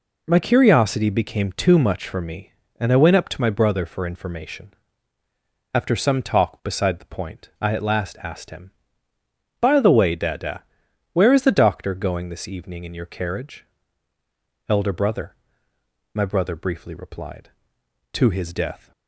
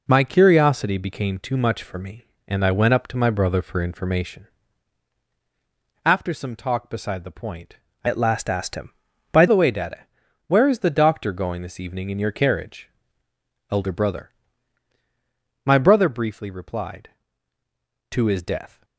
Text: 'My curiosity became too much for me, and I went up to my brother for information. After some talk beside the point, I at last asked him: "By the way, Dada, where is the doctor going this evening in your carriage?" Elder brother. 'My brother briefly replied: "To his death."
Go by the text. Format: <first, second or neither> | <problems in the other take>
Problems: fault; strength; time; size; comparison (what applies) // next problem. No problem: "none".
first | changes voice from "at" to "By"; from 8.0 to 9.4 s; 1.4 s long